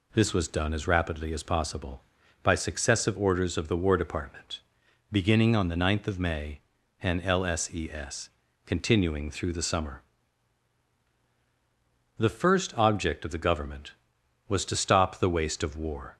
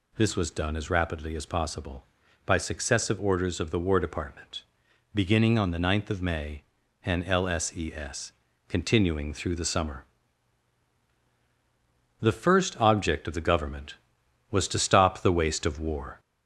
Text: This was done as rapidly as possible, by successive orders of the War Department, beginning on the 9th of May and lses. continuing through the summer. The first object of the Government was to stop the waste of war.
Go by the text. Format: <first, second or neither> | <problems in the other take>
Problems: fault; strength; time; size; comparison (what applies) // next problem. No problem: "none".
first | gets louder; slight; throughout; 2.5 dB